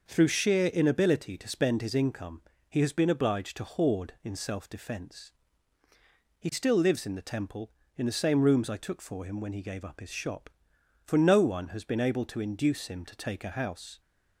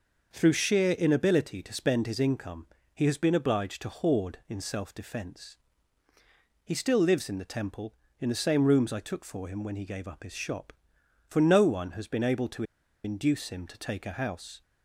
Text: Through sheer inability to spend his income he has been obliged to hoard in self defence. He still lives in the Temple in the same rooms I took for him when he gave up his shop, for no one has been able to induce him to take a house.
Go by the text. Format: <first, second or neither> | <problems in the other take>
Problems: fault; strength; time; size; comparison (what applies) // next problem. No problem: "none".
first | pauses between "income" and "he"; slight; at 2.6 s; 0.26 s long; slight in the first // pauses between "to" and "induce"; at 12.6 s; 0.41 s long